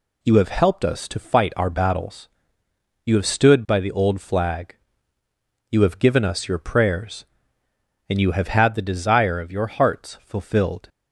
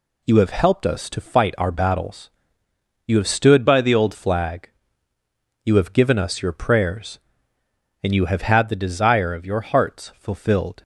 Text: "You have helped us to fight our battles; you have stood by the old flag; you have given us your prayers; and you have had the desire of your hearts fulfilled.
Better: first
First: none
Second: changes voice from "by" to "old"; from 3.6 to 4.1 s; 0.5 s long

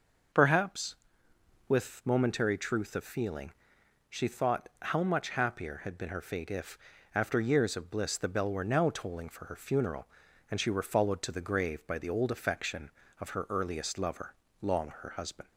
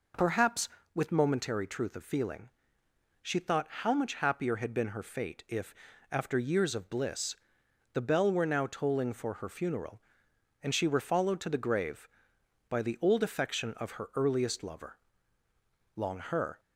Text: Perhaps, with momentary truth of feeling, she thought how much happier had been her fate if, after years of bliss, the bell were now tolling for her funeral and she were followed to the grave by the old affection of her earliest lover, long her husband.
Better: first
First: none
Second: stops before "husband"; at 16.5 s

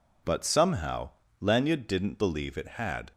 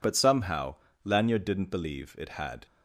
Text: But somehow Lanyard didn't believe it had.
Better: neither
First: pauses between "somehow" and "Lanyard"; slight; at 1.0 s; 0.30 s long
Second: pauses between "somehow" and "Lanyard"; slight; at 0.7 s; 0.30 s long

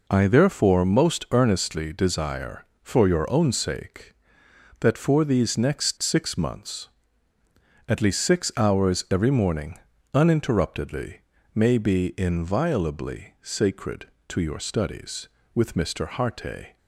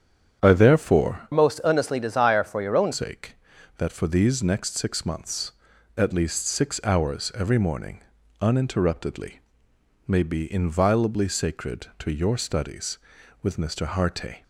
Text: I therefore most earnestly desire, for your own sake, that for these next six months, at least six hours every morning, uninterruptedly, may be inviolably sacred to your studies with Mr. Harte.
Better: first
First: none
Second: starts louder than the rest; strong; until 1.4 s; 8.5 dB // changes voice from "most" to "own"; from 1.3 to 2.9 s; 1.6 s long

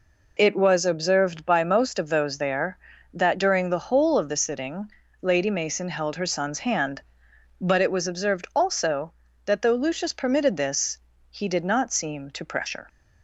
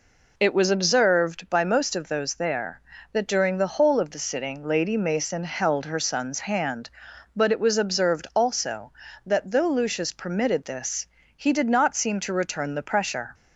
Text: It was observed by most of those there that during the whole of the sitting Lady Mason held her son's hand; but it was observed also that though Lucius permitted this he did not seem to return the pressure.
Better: second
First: pauses between "sitting" and "Lady"; slight; at 4.8 s; 0.32 s long // pauses between "this" and "he"; slight; at 10.9 s; 0.34 s long // skips "return the"; at 12.4 s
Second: pauses between "this" and "he"; slight; at 11.0 s; 0.32 s long

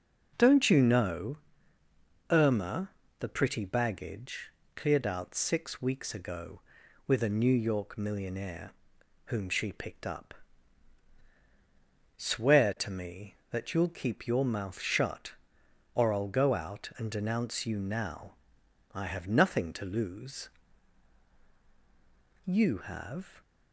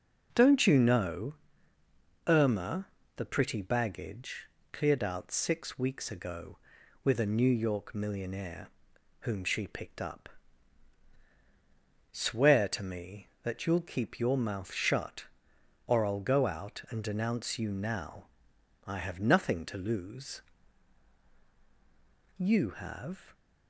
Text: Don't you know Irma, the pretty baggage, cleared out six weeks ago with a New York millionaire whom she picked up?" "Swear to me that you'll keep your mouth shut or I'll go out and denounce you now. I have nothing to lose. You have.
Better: neither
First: pauses between "know" and "Irma"; noticeable; at 1.3 s; 0.92 s long // pauses between "millionaire" and "whom"; noticeable; at 8.7 s; 0.54 s long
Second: pauses between "know" and "Irma"; noticeable; at 1.3 s; 0.92 s long // pauses between "millionaire" and "whom"; noticeable; at 8.6 s; 0.52 s long

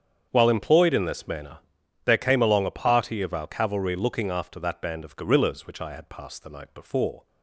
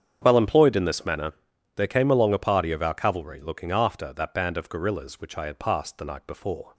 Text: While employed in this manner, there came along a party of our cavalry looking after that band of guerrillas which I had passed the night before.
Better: neither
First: starts louder than the rest; strong; until 1.3 s; 8 dB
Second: starts louder than the rest; strong; until 1.2 s; 8 dB

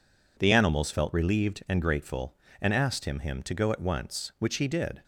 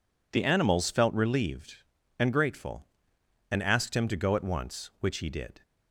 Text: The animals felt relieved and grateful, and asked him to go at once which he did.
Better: second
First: says "him" twice; at 3.1 s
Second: none

